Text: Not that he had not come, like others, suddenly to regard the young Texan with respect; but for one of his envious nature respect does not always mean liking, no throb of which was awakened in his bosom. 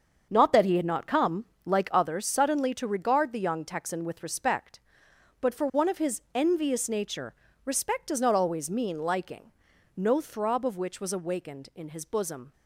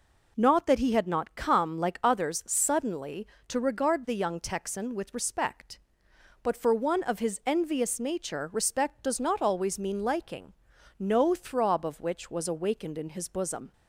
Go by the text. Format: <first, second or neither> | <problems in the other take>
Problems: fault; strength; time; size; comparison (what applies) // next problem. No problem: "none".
second | starts louder than the rest; until 1.8 s; 6.5 dB // pauses between "nature" and "respect"; slight; at 7.3 s; 0.30 s long